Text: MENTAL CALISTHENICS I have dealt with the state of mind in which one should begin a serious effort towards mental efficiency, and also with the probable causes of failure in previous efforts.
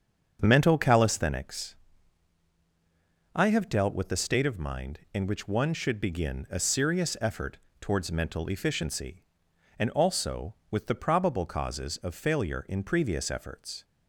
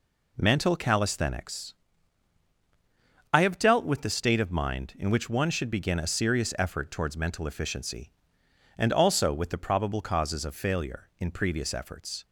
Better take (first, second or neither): second